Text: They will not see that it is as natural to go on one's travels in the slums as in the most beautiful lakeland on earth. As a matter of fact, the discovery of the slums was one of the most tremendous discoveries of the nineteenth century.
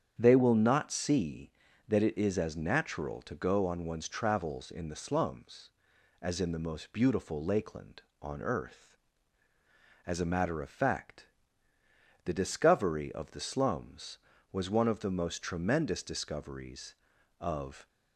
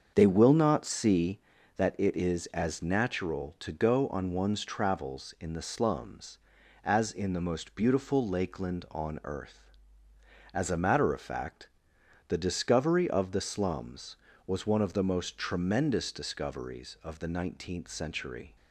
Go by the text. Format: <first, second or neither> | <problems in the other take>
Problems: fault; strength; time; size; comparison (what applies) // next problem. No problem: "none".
second | starts louder than the rest; strong; until 1.2 s; 8.5 dB; also in the second // stops before "the nineteenth century"; at 17.8 s